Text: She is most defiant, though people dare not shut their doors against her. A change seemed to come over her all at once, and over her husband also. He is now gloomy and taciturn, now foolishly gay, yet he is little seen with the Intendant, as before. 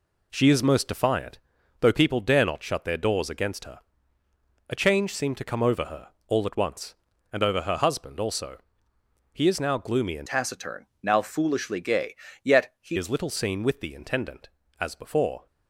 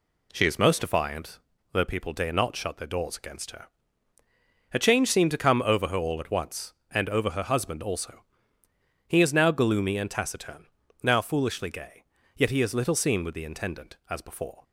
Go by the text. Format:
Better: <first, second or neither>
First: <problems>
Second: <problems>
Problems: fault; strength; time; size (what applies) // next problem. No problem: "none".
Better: second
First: pauses between "her" and "all"; slight; at 6.0 s; 0.20 s long // changes voice from "taciturn" to "he"; from 10.2 to 12.9 s; 2.7 s long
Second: none